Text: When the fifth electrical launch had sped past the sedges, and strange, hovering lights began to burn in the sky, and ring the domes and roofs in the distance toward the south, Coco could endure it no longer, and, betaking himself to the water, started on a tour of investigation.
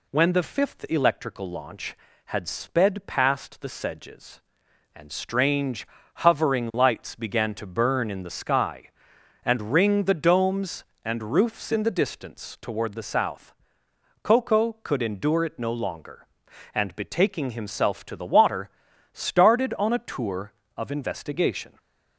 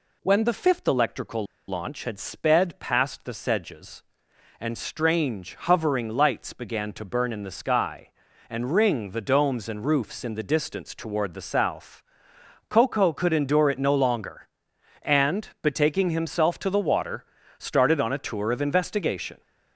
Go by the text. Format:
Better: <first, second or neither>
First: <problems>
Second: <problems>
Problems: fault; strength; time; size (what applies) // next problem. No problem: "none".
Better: first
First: none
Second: pauses between "electrical" and "launch"; slight; at 1.4 s; 0.23 s long